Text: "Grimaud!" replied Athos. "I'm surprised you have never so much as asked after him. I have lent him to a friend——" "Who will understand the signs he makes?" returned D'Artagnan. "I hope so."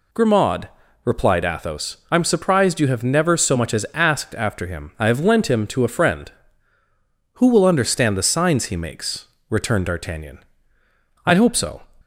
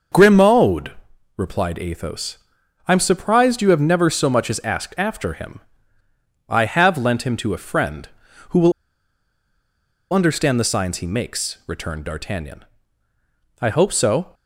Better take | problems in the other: first | starts louder than the rest; noticeable; until 1.5 s; 6 dB // pauses between "will" and "understand"; strong; at 8.7 s; 1.4 s long

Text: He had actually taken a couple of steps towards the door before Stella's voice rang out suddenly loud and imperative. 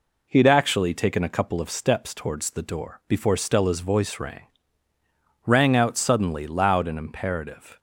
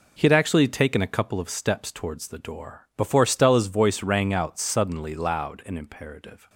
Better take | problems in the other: second | says "rang" twice; at 5.4 s

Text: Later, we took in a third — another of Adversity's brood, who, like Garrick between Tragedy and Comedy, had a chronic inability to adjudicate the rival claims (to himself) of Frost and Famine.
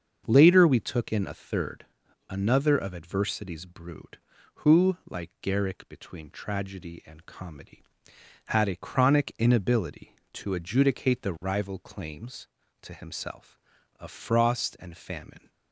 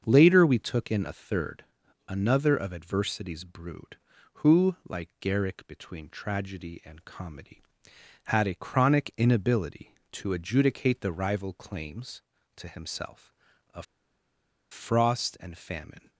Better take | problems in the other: first | starts louder than the rest; until 1.0 s; 7 dB; also in the first // pauses between "of" and "Frost"; noticeable; at 13.8 s; 0.86 s long

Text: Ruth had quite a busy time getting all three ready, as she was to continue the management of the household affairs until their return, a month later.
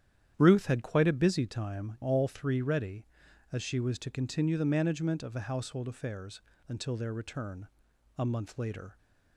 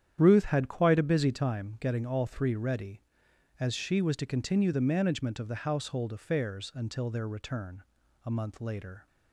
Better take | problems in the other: second | starts louder than the rest; strong; until 1.3 s; 10 dB; strong in the second // skips "getting"; at 1.9 s // pauses between "affairs" and "until"; slight; at 6.4 s; 0.26 s long

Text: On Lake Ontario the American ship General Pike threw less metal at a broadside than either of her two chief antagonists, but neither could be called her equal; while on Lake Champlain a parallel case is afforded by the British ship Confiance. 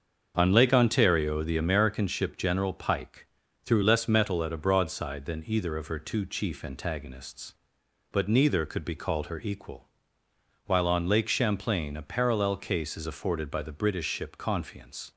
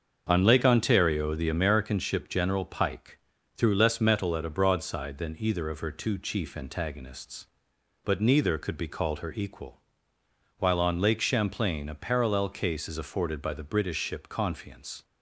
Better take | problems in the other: neither | starts louder than the rest; the same in both // pauses between "Pike" and "threw"; the same in both

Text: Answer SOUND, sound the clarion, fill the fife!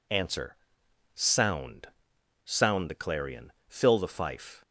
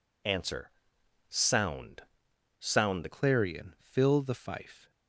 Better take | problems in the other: first | pauses between "Answer" and "SOUND"; noticeable; at 0.7 s; 0.58 s long; noticeable in the first // changes voice at "clarion"; from 3.1 s on; 1.8 s long

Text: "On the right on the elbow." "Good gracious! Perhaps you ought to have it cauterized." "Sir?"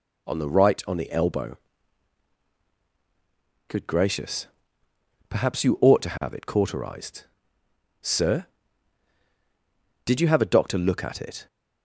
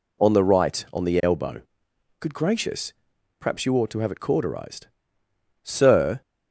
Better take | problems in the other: second | goes on to say "Did you have a doctor look at it"; from 10.0 s on; 1.4 s long

